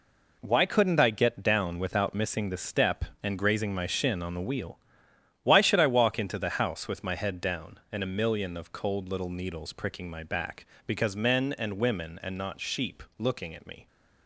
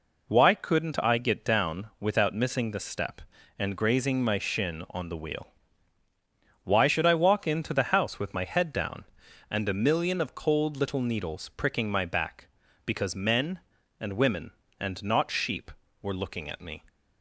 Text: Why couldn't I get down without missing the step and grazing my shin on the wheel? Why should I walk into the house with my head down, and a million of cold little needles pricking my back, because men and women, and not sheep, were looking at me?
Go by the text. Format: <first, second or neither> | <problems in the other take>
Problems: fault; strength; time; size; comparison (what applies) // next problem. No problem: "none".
second | skips "were"; at 13.0 s